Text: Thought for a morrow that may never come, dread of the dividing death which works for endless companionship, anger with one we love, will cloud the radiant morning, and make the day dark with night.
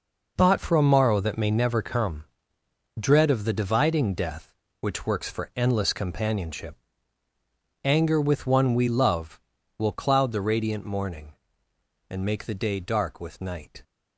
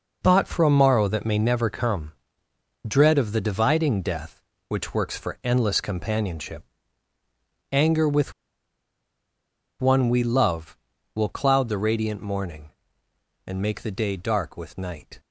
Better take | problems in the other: first | pauses between "with" and "one"; strong; at 8.3 s; 1.4 s long

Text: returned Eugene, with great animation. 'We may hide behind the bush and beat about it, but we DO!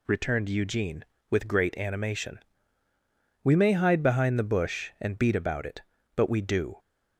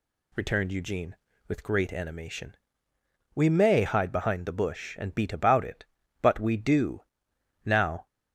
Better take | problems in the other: first | goes on to say "Now"; slight; from 7.6 s on; 0.40 s long

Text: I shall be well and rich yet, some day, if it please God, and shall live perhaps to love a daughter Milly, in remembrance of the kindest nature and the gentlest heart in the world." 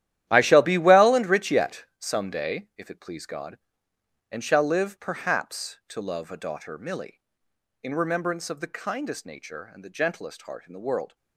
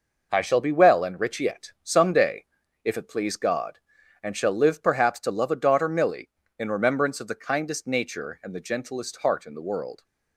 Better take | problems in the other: second | gets quieter; strong; throughout; 13.5 dB

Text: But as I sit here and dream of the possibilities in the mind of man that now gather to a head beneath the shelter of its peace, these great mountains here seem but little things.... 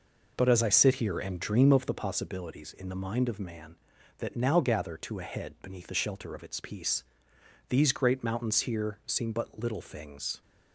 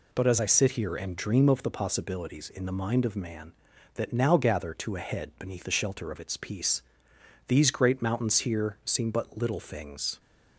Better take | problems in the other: second | starts louder than the rest; noticeable; until 2.2 s; 5 dB

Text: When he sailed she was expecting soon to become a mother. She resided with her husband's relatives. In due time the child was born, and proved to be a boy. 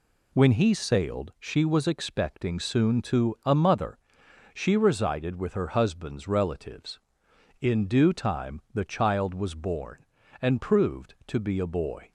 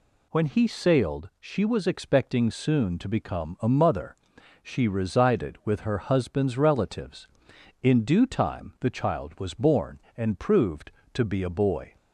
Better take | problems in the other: second | skips "become"; at 3.3 s

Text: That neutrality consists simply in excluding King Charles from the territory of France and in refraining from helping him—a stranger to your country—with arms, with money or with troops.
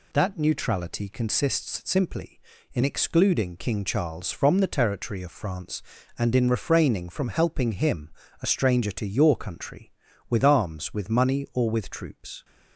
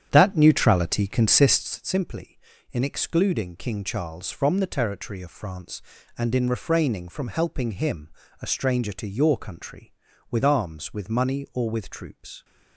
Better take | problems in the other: first | starts louder than the rest; strong; until 1.7 s; 9 dB

